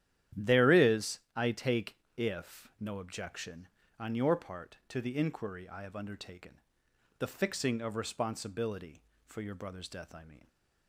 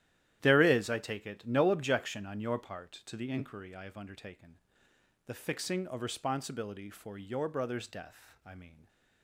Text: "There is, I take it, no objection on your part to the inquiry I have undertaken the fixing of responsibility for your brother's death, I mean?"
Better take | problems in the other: second | starts louder than the rest; strong; until 1.5 s; 11 dB; strong in the second // says "if" for "it"; at 2.1 s // pauses between "undertaken" and "the"; noticeable; at 6.5 s; 0.60 s long; noticeable in the second

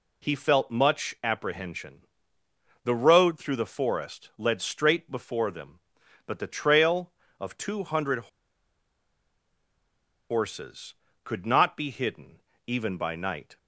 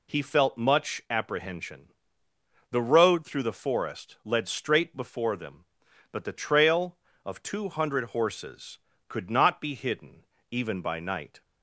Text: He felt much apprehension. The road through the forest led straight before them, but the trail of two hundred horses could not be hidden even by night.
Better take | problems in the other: second | pauses between "hundred" and "horses"; strong; at 8.1 s; 2.1 s long // pauses between "hidden" and "even"; slight; at 12.3 s; 0.26 s long; slight in the second

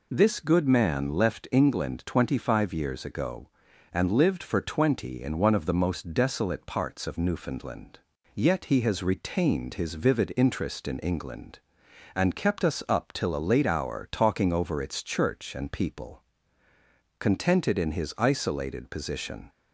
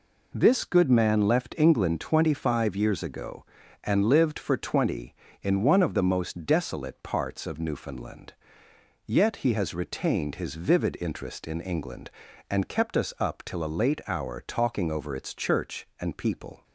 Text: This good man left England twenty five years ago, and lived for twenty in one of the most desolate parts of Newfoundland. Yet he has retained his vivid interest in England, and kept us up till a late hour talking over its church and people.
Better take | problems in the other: second | goes on to say "Contented in his isolated position"; strong; from 17.1 s on; 2.3 s long

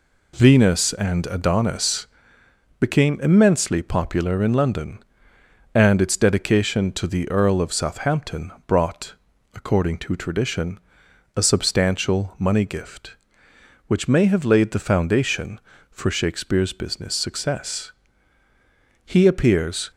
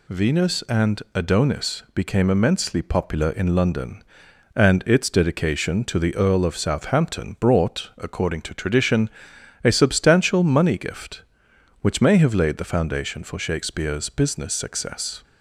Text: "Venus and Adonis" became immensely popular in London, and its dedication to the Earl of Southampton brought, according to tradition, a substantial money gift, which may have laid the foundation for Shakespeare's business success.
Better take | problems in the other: second | pauses between "Adonis" and "became"; noticeable; at 2.0 s; 0.74 s long // pauses between "Southampton" and "brought"; slight; at 8.5 s; 0.16 s long // goes on to say "He appears"; noticeable; from 19.0 s on; 0.86 s long

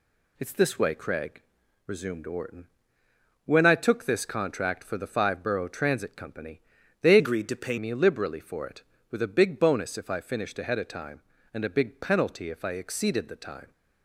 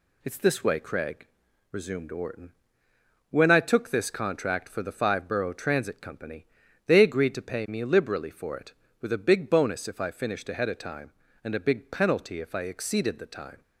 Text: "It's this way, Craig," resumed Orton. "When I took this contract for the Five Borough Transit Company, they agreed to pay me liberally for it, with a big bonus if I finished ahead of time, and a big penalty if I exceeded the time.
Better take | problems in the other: second | changes voice from "agreed" to "pay"; from 7.1 to 7.7 s; 0.6 s long

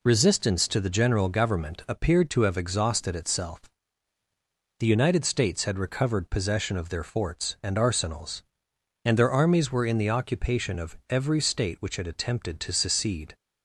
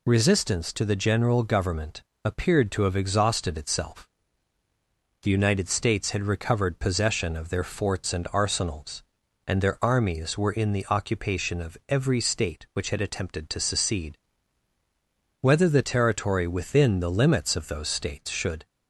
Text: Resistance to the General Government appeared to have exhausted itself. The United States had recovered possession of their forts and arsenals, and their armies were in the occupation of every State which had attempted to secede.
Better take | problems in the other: first | pauses between "Government" and "appeared"; slight; at 2.0 s; 0.24 s long // goes on to say "Whether the territory within the limits of those States should"; strong; from 15.3 s on; 3.2 s long

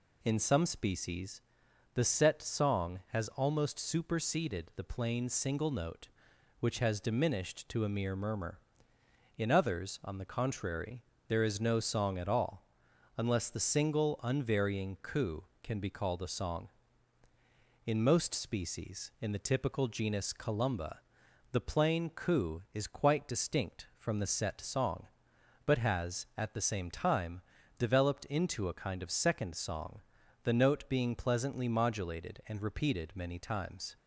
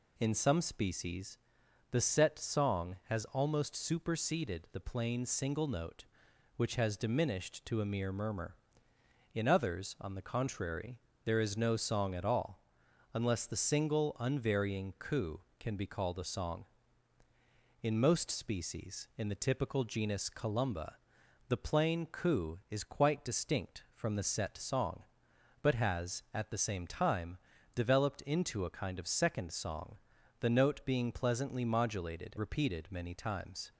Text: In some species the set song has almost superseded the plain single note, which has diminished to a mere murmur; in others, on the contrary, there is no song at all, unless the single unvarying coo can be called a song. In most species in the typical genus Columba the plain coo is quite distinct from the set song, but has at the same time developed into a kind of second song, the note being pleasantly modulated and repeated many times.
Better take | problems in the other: first | pauses between "species" and "the"; noticeable; at 1.3 s; 0.54 s long; noticeable in the first // pauses between "Columba" and "the"; noticeable; at 20.9 s; 0.52 s long; noticeable in the first // pauses between "time" and "developed"; at 27.3 s; 0.38 s long; also in the first // skips "and"; at 32.3 s

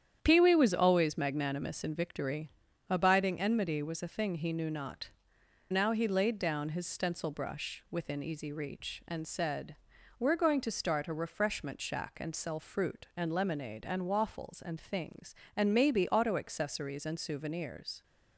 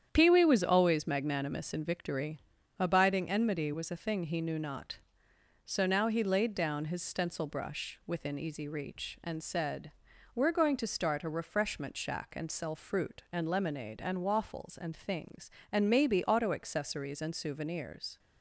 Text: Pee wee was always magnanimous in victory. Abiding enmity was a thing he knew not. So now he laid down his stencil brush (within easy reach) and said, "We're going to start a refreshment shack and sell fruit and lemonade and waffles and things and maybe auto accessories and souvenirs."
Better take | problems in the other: second | starts louder than the rest; strong; until 1.2 s; 9.5 dB; strong in the second // skips "So"; at 5.3 s

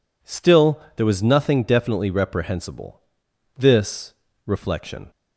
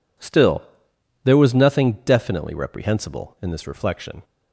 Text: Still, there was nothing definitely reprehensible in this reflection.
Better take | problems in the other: second | skips "in"; at 3.2 s // pauses between "this" and "reflection"; slight; at 4.1 s; 0.32 s long

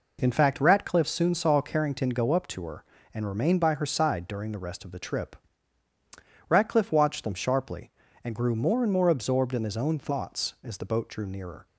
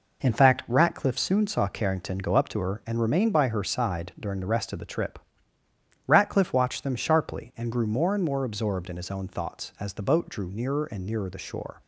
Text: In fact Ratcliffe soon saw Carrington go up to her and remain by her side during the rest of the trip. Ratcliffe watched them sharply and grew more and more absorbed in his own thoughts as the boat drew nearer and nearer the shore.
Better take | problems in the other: second | stops before "and nearer the shore"; at 11.6 s

